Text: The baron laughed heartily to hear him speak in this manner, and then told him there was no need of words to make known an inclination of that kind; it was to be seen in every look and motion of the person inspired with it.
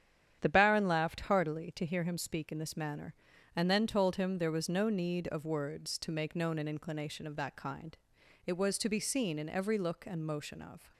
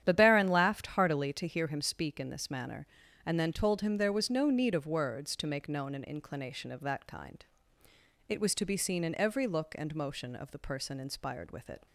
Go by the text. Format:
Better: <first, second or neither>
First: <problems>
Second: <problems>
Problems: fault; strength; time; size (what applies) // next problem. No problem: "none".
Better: second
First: starts louder than the rest; strong; until 1.4 s; 9.5 dB // stops before "the person inspired with it"; at 10.9 s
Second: starts louder than the rest; strong; until 1.0 s; 10 dB